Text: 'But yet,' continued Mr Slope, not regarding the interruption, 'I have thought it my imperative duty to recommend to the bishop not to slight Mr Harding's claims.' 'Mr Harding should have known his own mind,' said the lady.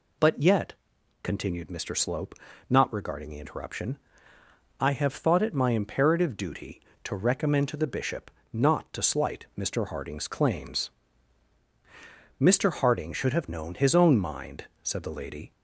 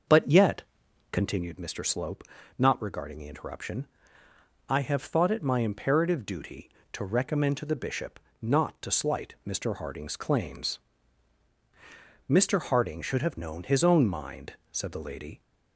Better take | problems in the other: first | starts louder than the rest; until 1.5 s; 6 dB // pauses between "bishop" and "not"; slight; at 8.1 s; 0.22 s long; slight in the first

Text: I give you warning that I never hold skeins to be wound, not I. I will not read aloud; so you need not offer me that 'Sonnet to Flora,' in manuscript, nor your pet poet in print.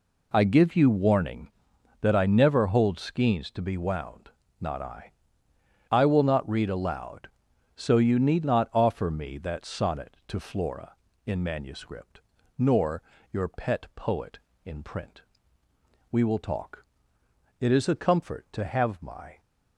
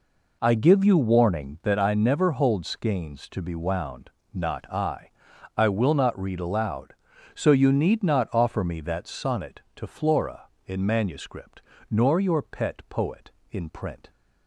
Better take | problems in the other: second | pauses between "nor" and "your"; slight; at 13.0 s; 0.28 s long // goes on to say "We will talk it is a comfort to have my"; strong; from 16.1 s on; 3.3 s long

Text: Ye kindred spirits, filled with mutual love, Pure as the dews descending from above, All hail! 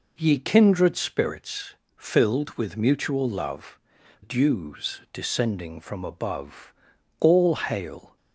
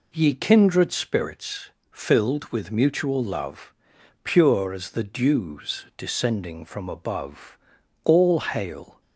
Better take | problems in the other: second | skips "Pure as the"; at 4.0 s

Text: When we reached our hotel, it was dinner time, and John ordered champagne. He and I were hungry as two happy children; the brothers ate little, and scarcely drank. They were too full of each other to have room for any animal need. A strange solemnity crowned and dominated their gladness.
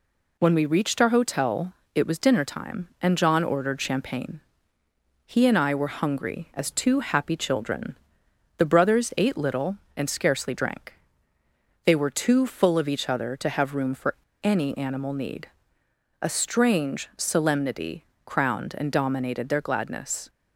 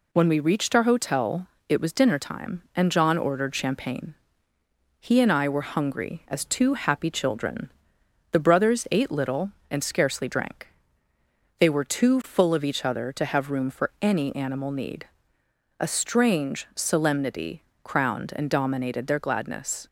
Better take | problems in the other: second | pauses between "for" and "any"; slight; at 14.1 s; 0.31 s long // pauses between "solemnity" and "crowned"; slight; at 18.0 s; 0.18 s long; slight in the second

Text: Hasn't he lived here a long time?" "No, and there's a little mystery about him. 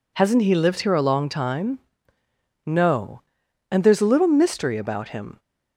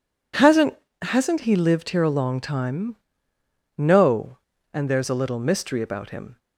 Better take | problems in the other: first | says "Hasn't" twice; at 1.0 s

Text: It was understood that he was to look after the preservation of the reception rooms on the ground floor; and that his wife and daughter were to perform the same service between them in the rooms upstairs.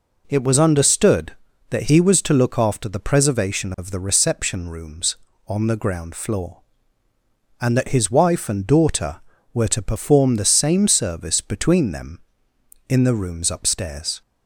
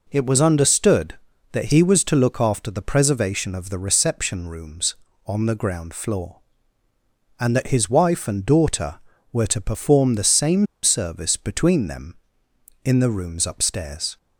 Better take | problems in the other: first | pauses between "same" and "service"; slight; at 10.6 s; 0.17 s long

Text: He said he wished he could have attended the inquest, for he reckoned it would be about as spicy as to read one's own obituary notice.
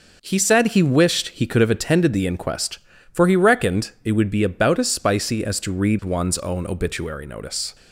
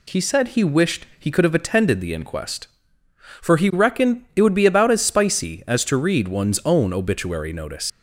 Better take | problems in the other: first | leaves "notice" unfinished; at 7.8 s; 120 ms

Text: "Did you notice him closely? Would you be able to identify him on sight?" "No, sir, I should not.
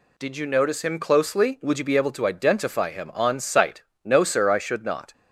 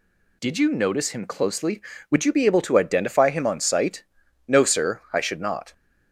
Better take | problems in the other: neither | none

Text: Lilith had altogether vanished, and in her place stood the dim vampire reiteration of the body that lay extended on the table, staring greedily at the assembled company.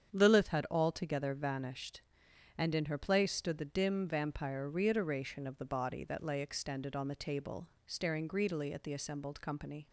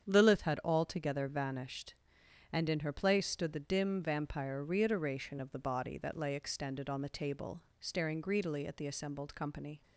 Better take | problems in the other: neither | starts louder than the rest; strong; the same in both

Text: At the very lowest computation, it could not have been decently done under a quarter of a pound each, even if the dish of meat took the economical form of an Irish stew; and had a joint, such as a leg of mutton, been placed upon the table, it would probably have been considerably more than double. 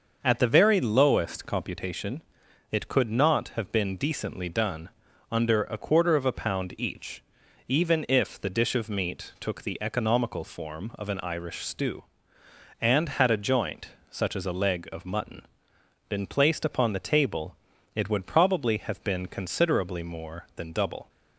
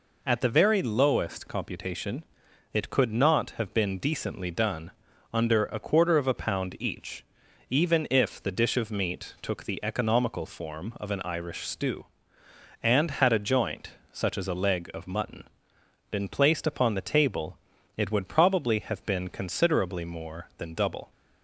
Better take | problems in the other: second | starts louder than the rest; until 1.9 s; 6.5 dB // pauses between "done" and "under"; at 4.9 s; 0.40 s long; also in the second

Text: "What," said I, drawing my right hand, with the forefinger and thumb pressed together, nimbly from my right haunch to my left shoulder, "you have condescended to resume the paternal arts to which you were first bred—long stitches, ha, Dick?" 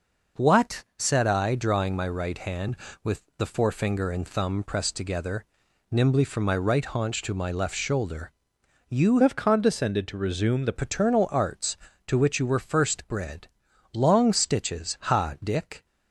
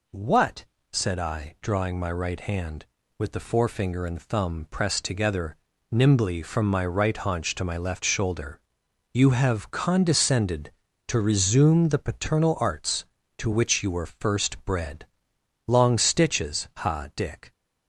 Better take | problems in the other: second | changes voice from "have" to "the"; from 9.2 to 10.7 s; 1.5 s long

